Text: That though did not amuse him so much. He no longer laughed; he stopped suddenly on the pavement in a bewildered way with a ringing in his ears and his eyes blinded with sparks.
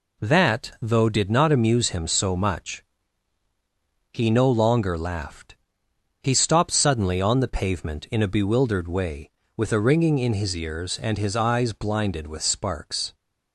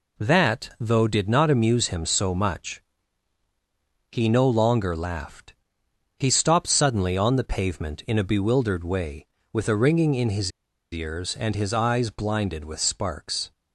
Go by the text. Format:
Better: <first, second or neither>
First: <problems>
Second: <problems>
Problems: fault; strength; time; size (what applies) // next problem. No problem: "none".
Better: first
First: none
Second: pauses between "his" and "ears"; at 10.5 s; 0.41 s long